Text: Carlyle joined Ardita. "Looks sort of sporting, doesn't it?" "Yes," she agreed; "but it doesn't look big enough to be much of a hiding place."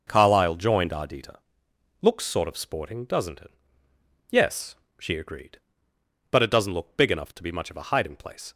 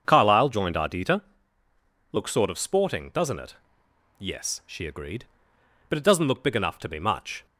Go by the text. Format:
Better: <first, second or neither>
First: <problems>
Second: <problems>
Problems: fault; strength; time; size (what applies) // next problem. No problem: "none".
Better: first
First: none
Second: starts louder than the rest; until 1.0 s; 6.5 dB // stops before "of a hiding place"; at 7.4 s